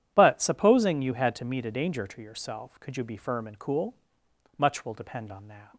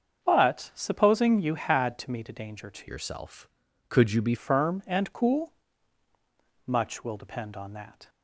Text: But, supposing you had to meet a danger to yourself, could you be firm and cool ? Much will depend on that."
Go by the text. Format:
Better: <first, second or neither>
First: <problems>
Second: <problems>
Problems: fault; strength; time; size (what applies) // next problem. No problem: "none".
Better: first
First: none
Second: starts louder than the rest; until 1.2 s; 7 dB // changes voice from "yourself" to "be"; from 2.8 to 4.3 s; 1.5 s long